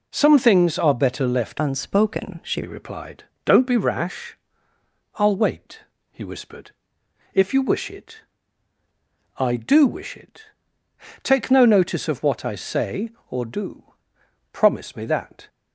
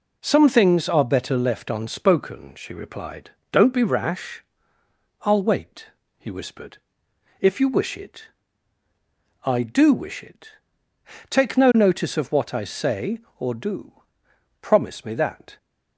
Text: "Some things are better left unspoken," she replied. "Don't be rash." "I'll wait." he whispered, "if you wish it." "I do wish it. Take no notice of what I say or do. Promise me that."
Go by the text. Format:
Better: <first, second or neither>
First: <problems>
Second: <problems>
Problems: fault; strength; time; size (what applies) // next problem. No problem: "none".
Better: second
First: changes voice from "unspoken" to "she"; from 1.5 to 2.6 s; 1.1 s long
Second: none